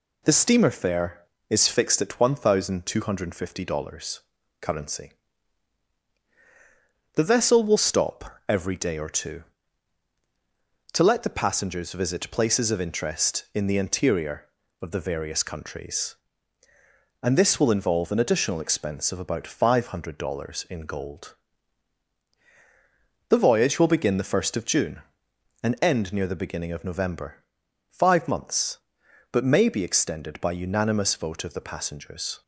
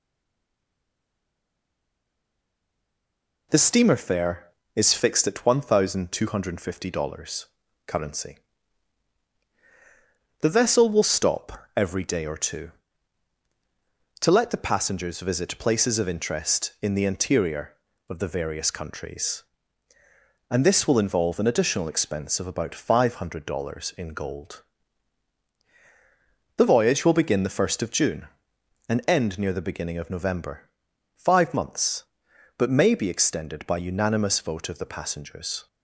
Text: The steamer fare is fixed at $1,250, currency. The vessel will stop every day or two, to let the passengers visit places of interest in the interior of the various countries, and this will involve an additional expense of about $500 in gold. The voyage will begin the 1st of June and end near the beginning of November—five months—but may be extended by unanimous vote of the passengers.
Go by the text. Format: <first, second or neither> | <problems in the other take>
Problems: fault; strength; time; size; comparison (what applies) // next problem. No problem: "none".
first | stays silent before the first word; strong; until 3.4 s; 3.4 s long